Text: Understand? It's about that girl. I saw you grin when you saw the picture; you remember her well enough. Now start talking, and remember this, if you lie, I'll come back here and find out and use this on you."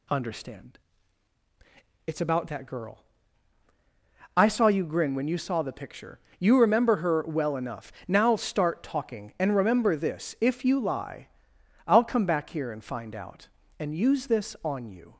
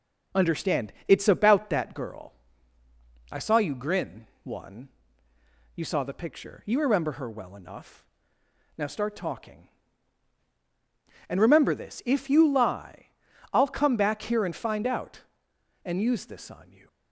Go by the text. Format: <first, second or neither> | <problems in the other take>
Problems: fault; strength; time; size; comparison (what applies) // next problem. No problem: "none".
first | says "one" for "when"; at 4.4 s